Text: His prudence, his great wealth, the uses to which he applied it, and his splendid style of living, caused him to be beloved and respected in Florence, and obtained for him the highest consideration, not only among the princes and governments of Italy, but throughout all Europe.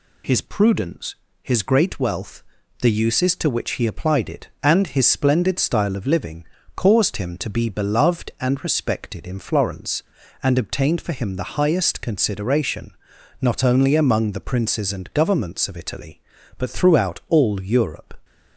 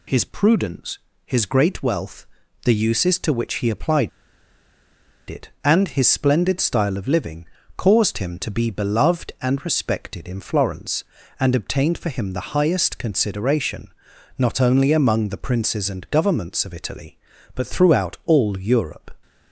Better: first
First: none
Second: pauses between "applied" and "it"; at 4.0 s; 1.1 s long

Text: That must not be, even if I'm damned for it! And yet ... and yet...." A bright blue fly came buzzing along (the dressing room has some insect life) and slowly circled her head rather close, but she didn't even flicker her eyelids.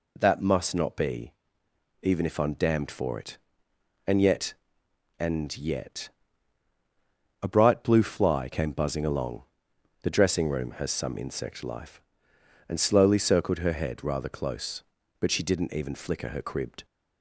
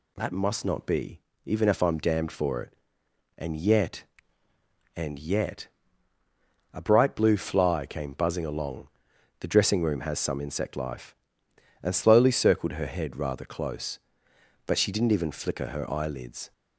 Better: second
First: says "cribbed" for "eyelids"; at 16.4 s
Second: none

